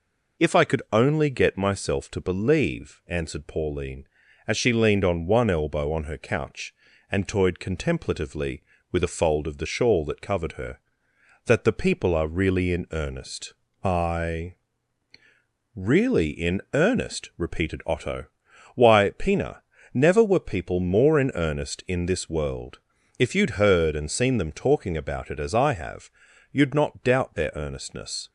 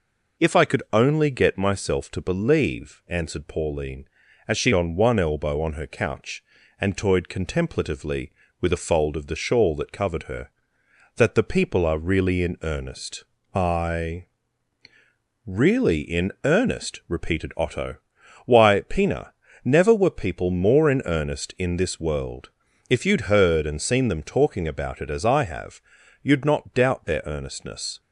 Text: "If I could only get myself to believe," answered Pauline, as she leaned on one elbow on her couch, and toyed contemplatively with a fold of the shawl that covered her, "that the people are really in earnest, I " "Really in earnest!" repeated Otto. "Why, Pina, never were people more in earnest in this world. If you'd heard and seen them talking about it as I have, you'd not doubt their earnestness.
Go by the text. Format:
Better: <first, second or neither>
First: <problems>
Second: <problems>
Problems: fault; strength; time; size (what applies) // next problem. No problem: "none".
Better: first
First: none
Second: skips "leaned"; at 4.7 s